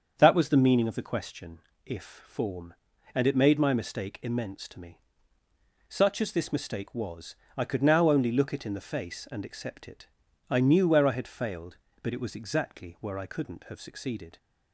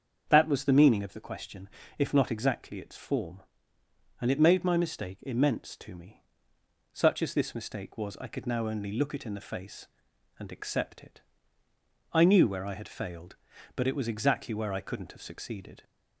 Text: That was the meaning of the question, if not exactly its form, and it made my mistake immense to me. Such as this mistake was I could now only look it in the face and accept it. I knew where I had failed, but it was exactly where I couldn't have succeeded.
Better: second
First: starts louder than the rest; until 1.1 s; 7 dB // skips "not exactly its"; at 2.2 s // pauses between "was" and "I"; slight; at 7.3 s; 0.22 s long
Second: starts louder than the rest; until 1.3 s; 7 dB

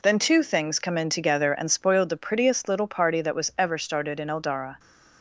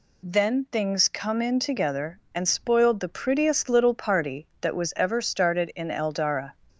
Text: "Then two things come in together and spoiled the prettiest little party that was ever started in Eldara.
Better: first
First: none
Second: skips "two"; at 0.6 s

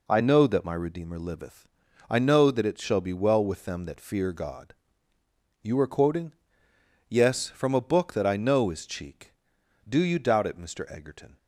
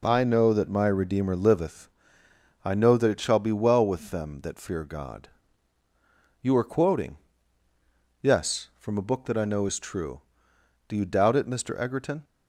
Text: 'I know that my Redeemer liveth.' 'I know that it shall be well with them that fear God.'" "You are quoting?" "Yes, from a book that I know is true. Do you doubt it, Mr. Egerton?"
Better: second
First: says "cheek" for "true"; at 8.8 s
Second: none

